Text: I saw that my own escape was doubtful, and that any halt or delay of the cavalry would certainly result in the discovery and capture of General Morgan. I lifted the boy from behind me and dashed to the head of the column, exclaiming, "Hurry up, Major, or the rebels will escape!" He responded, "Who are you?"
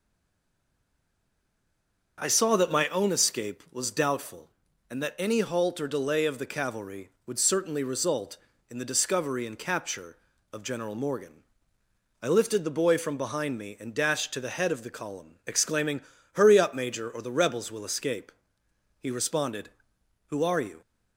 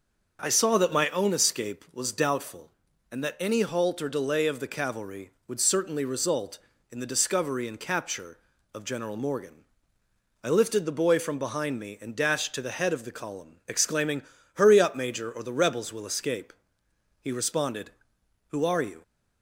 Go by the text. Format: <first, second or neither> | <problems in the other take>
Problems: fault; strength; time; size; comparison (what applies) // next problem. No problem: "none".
second | stays silent before the first word; until 2.1 s; 2.1 s long // starts louder than the rest; until 3.2 s; 6 dB; also in the second